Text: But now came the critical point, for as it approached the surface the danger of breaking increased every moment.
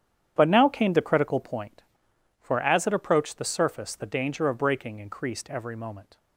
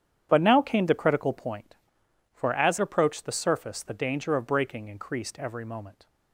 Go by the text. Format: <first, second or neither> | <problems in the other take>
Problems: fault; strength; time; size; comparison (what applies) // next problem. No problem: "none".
first | starts louder than the rest; strong; until 1.3 s; 9.5 dB; strong in the first // skips "it"; at 2.7 s